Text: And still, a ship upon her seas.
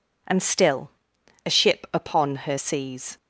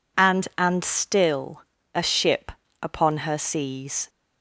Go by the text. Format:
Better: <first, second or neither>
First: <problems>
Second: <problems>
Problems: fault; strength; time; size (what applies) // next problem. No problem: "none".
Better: first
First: none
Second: says "And" twice; at 0.5 s // pauses between "ship" and "upon"; slight; at 2.5 s; 0.32 s long